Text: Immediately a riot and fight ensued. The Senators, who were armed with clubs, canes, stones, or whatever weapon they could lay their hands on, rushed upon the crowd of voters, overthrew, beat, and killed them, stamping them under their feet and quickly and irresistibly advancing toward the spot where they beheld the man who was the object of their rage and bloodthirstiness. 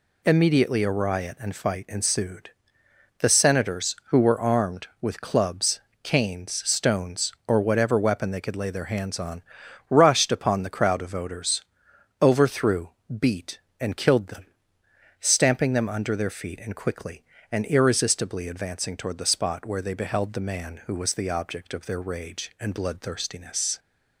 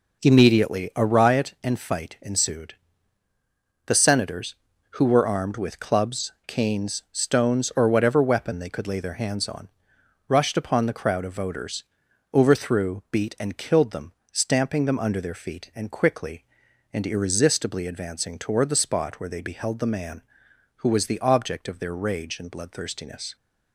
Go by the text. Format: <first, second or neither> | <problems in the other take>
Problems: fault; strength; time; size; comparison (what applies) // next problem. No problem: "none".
neither | none